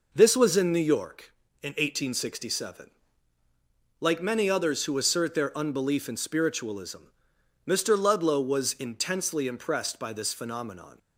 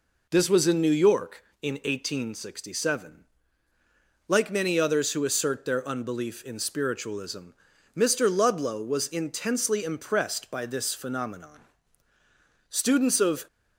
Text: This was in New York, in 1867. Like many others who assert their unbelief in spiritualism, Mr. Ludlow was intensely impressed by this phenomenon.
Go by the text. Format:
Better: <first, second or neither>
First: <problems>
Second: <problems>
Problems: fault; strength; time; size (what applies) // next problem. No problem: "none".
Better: first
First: none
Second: goes on to say "Students of"; noticeable; from 12.6 s on; 0.78 s long